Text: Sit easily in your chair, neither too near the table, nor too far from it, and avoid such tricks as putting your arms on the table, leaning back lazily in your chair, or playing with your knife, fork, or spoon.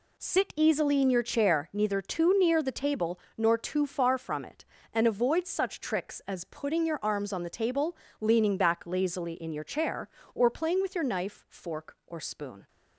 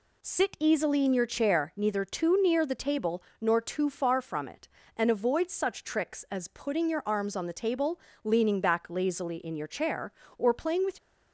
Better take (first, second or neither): first